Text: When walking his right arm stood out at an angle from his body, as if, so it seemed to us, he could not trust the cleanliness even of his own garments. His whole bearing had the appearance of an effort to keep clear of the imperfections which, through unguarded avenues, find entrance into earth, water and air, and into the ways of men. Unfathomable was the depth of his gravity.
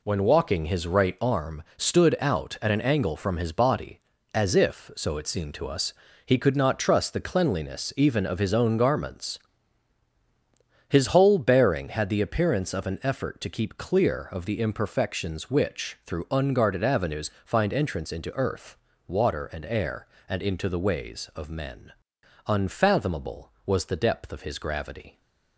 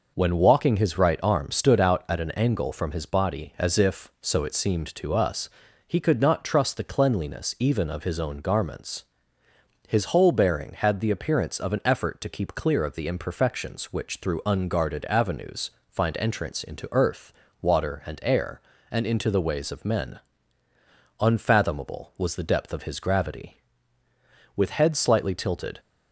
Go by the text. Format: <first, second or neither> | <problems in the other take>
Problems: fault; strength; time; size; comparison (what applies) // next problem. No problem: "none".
first | goes on to say "With head slightly tilted"; noticeable; from 24.5 s on; 1.2 s long